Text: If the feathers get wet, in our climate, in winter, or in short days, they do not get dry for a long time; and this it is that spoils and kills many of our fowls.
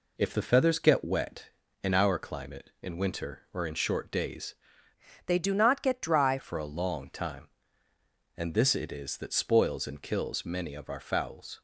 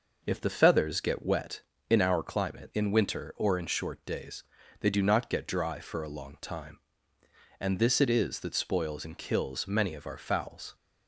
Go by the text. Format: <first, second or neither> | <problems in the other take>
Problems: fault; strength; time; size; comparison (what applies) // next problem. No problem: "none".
second | changes voice from "they" to "dry"; from 5.2 to 6.3 s; 1.1 s long